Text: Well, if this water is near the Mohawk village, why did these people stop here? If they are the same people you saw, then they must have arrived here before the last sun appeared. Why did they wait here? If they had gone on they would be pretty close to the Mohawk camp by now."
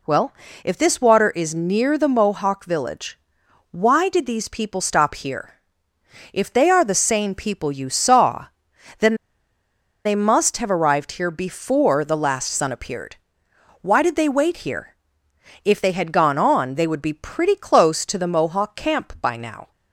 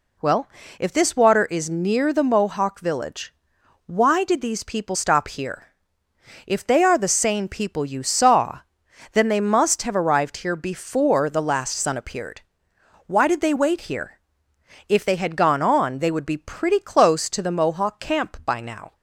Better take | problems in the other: second | pauses between "then" and "they"; noticeable; at 9.1 s; 0.91 s long

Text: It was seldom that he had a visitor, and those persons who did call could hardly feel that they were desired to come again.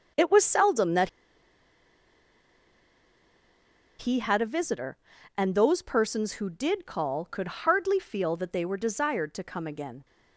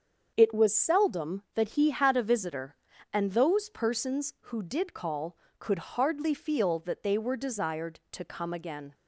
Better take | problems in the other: second | starts louder than the rest; until 4.0 s; 6.5 dB; also in the second // pauses between "that" and "he"; strong; at 1.0 s; 2.8 s long

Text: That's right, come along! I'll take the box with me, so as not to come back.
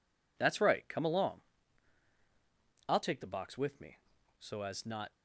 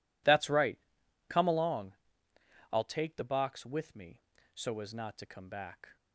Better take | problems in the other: second | stops before "to come back"; at 5.1 s

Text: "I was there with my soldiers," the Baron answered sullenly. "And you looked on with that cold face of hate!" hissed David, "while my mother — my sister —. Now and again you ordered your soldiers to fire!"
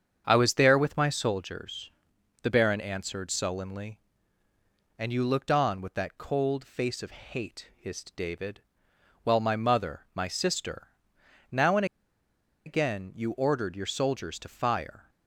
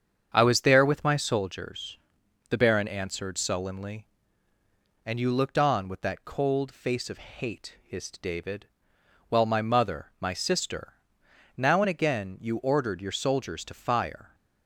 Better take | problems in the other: second | starts louder than the rest; strong; until 1.2 s; 7.5 dB; strong in the second // pauses between "and" and "again"; noticeable; at 11.8 s; 0.81 s long

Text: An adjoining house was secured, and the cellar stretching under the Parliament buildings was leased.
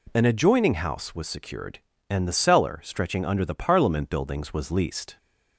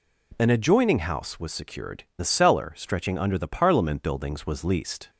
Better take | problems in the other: first | skips "and"; at 2.1 s

